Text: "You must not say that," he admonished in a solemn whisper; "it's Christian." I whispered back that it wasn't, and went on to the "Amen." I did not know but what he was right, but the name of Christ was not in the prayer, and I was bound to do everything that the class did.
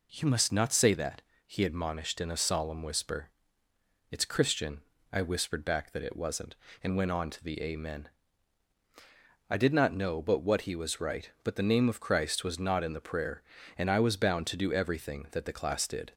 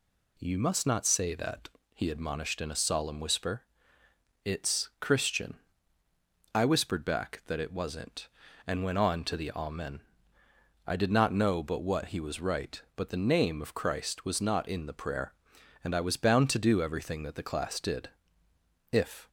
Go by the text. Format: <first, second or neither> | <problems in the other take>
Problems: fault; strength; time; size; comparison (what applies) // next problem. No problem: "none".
first | goes on to say "If"; slight; from 18.9 s on; 0.36 s long